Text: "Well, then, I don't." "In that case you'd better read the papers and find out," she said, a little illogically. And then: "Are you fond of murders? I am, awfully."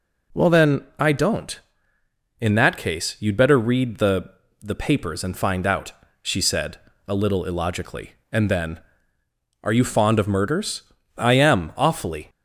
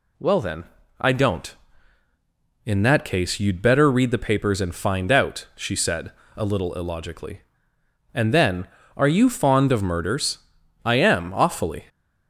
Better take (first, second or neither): second